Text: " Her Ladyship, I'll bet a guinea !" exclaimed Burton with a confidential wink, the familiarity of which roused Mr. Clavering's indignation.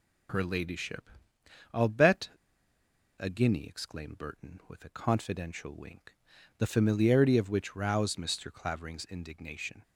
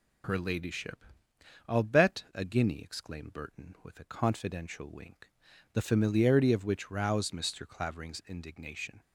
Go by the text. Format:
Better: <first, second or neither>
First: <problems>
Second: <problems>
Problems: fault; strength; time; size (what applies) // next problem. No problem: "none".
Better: second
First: pauses between "bet" and "a"; noticeable; at 2.2 s; 0.89 s long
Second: none